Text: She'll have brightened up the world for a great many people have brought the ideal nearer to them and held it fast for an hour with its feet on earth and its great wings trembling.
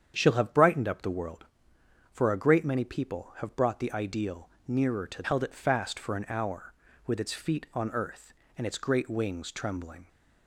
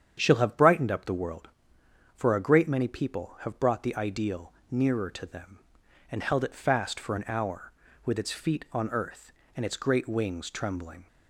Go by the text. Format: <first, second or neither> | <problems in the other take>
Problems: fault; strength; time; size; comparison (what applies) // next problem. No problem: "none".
second | starts louder than the rest; strong; until 1.1 s; 8.5 dB; strong in the second // pauses between "ideal" and "nearer"; slight; at 4.4 s; 0.16 s long; slight in the second // skips "them and"; at 5.2 s